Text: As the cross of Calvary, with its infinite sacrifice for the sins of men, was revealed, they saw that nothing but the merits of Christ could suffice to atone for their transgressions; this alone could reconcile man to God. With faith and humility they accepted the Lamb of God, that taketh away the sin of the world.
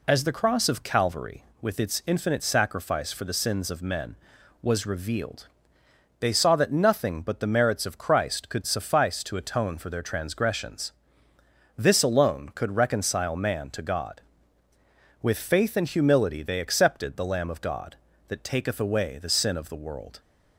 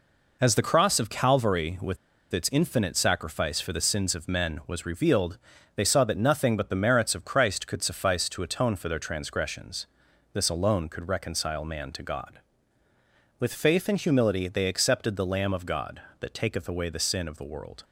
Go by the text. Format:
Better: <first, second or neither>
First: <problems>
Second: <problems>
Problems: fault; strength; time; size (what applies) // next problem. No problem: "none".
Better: first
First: none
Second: pauses between "with" and "its"; slight; at 1.9 s; 0.35 s long